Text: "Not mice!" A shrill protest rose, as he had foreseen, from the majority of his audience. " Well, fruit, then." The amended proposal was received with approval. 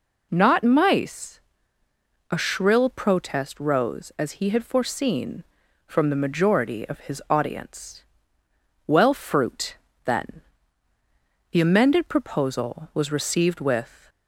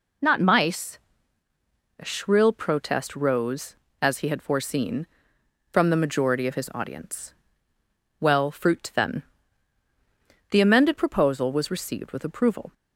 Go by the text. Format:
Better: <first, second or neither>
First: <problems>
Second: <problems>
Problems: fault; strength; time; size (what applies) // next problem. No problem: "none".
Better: second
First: stops before "approval"; at 14.0 s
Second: none